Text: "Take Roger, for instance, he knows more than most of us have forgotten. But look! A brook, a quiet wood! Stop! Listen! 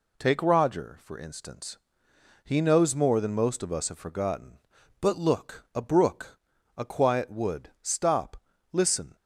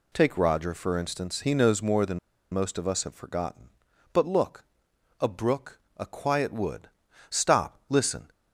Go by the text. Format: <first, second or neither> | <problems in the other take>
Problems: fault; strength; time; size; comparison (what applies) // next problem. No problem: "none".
first | pauses between "than" and "most"; slight; at 2.1 s; 0.34 s long